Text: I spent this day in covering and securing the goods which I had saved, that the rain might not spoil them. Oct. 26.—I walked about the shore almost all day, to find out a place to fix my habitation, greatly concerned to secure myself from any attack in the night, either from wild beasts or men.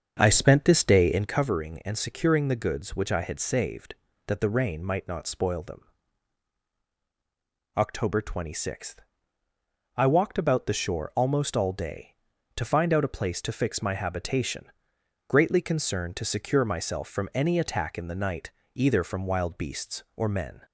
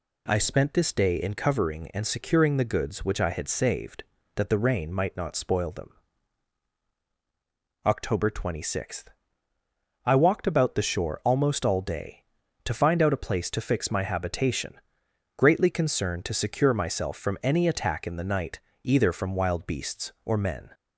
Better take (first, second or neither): second